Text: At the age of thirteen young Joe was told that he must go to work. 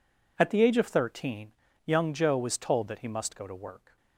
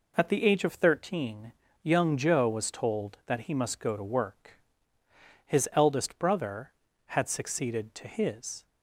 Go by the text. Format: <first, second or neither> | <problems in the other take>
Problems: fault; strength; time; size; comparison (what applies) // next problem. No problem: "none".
first | pauses between "thirteen" and "young"; slight; at 1.5 s; 0.32 s long; slight in the first // goes on to say "His eldest brother had succeeded to his"; strong; from 5.4 s on; 3.2 s long